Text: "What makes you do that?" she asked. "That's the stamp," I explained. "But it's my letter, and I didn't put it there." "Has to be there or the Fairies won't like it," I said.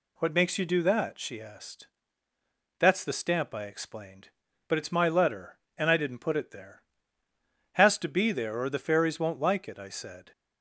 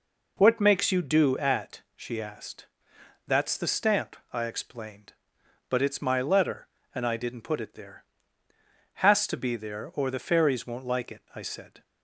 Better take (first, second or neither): first